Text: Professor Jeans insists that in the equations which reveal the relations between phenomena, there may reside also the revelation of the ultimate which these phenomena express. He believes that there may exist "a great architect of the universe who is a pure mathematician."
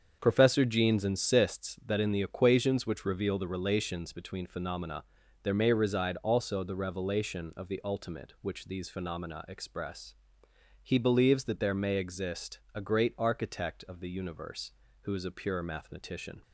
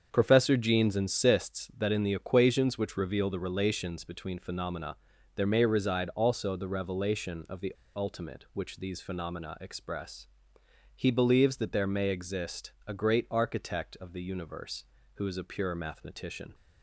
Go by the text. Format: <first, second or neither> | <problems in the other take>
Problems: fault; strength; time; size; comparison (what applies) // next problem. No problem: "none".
first | starts louder than the rest; strong; until 1.1 s; 7 dB; strong in the first // pauses between "the" and "ultimate"; slight; at 7.7 s; 0.23 s long // pauses between "exist" and "a"; slight; at 12.7 s; 0.16 s long; slight in the first